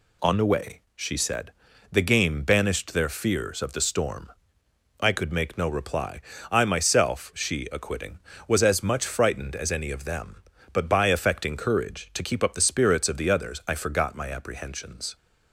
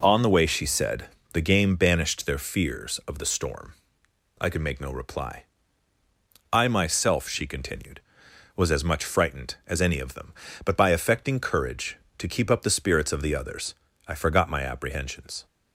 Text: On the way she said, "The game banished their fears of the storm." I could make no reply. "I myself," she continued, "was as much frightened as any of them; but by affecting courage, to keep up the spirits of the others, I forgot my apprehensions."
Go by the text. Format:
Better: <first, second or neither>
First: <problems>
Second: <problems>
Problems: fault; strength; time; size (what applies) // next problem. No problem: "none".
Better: second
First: pauses between "way" and "she"; slight; at 0.8 s; 0.16 s long // says "acquitting" for "continued"; at 7.7 s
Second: none